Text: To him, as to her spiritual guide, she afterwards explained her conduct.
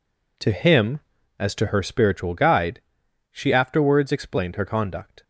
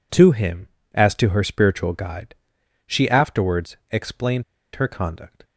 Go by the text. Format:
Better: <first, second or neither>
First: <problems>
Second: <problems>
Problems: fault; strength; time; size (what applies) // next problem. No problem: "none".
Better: first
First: none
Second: pauses between "explained" and "her"; slight; at 4.4 s; 0.32 s long